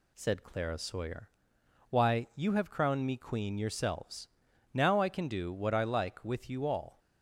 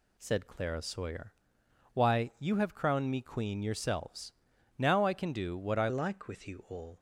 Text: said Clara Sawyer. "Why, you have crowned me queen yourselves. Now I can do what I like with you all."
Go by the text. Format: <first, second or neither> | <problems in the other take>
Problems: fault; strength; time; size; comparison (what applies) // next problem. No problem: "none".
first | changes voice at "like"; from 5.8 s on; 1.1 s long